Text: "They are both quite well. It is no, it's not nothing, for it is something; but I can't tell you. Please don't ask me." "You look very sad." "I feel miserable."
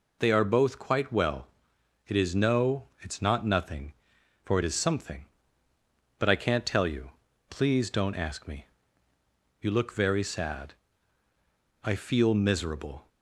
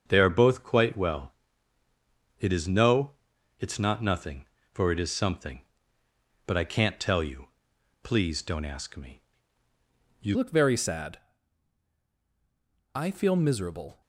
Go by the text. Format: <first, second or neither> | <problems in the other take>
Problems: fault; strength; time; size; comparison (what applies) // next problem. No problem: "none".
first | starts louder than the rest; until 1.0 s; 7 dB // changes voice at "look"; from 10.3 s on; 3.7 s long